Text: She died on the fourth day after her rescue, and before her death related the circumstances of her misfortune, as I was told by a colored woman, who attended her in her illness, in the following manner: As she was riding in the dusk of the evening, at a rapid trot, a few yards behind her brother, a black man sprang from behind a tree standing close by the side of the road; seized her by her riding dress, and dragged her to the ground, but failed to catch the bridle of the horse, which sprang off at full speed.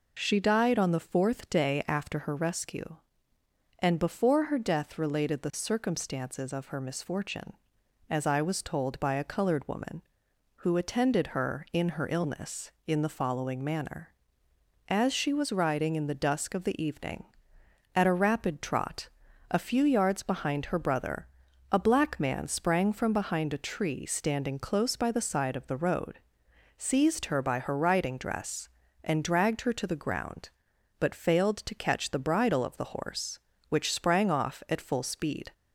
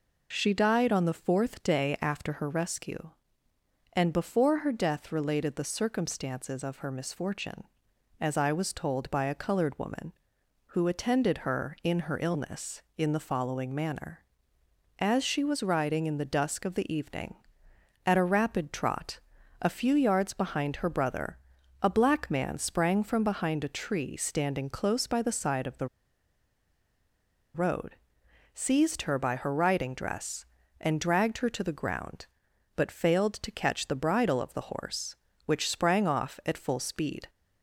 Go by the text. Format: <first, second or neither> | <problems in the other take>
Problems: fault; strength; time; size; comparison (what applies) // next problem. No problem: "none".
first | pauses between "the" and "road"; strong; at 25.8 s; 1.6 s long